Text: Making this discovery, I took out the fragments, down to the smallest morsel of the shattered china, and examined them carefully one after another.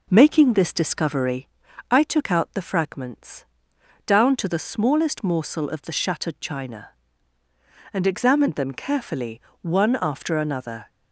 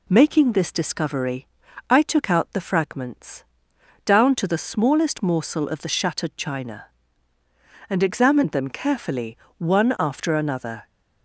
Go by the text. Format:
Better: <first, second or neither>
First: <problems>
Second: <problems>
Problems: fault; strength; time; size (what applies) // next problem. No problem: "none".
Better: second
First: starts louder than the rest; noticeable; until 1.5 s; 4 dB // pauses between "carefully" and "one"; slight; at 9.3 s; 0.22 s long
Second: pauses between "carefully" and "one"; slight; at 9.3 s; 0.22 s long